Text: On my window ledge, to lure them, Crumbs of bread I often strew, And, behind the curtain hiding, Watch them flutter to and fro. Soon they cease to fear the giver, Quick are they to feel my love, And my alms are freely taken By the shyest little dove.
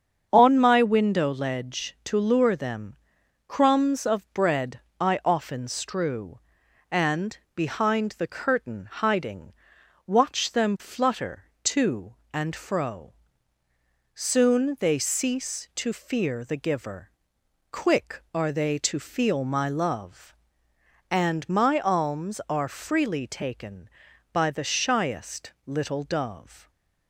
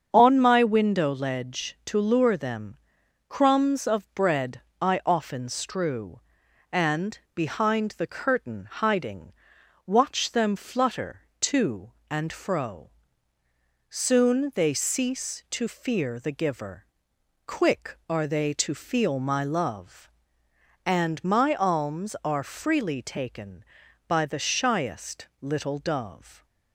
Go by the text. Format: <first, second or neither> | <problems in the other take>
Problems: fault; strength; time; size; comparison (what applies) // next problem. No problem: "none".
neither | starts louder than the rest; strong; the same in both // pauses between "bread" and "I"; slight; the same in both